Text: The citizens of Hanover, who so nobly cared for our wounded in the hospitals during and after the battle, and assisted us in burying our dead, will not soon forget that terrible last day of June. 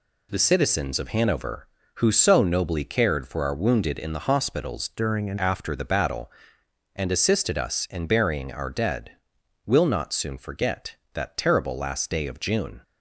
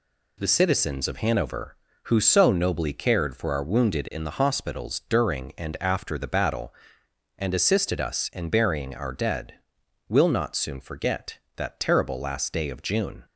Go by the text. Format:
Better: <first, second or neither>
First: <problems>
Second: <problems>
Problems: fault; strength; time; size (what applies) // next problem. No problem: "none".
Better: second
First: changes voice from "during" to "and"; from 4.9 to 5.3 s; 0.4 s long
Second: none